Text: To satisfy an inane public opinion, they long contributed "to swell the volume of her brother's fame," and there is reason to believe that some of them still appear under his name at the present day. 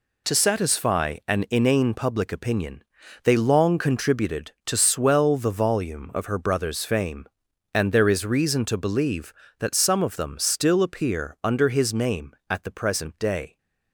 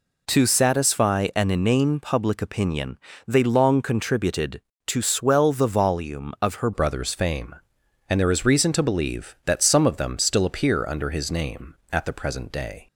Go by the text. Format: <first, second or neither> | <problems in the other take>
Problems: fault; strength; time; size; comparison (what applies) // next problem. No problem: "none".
first | changes voice at "brother's"; from 6.7 s on; 6.1 s long